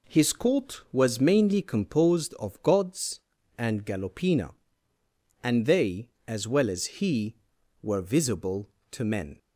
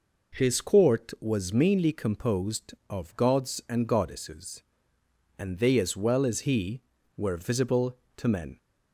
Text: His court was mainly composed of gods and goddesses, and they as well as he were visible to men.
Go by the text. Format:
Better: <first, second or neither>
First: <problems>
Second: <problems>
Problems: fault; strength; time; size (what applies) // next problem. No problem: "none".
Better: second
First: says "galopina" for "goddesses"; at 3.8 s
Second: none